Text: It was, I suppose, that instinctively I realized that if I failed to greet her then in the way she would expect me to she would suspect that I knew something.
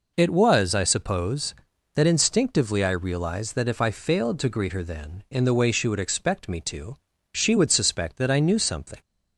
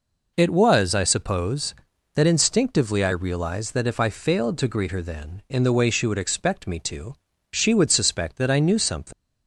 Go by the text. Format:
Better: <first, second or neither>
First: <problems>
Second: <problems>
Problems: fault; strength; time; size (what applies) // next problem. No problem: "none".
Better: first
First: pauses between "to" and "she"; at 6.9 s; 0.38 s long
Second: pauses between "to" and "she"; at 7.1 s; 0.38 s long // leaves "something" unfinished; at 9.1 s; 75 ms